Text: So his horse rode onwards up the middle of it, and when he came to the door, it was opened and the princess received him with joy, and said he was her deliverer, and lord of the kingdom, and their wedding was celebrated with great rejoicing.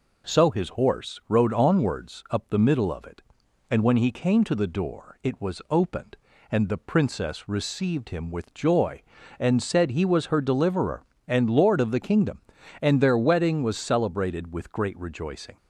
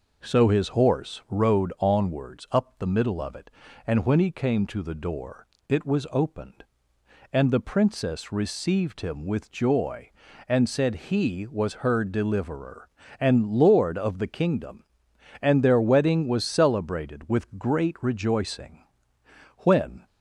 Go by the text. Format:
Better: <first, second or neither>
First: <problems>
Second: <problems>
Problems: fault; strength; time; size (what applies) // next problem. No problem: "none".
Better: first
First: none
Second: goes on to say "When"; slight; from 19.5 s on; 0.48 s long